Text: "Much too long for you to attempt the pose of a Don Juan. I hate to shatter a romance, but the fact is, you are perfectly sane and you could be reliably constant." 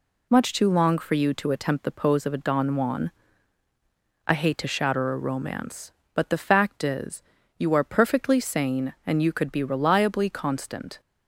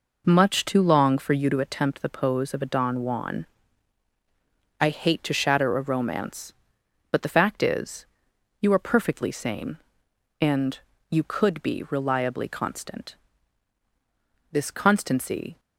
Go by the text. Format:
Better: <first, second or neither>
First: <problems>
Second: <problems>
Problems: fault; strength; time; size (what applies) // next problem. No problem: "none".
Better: first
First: none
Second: pauses between "and" and "you"; slight; at 10.7 s; 0.32 s long // goes on to say "This constancy"; noticeable; from 14.5 s on; 1.0 s long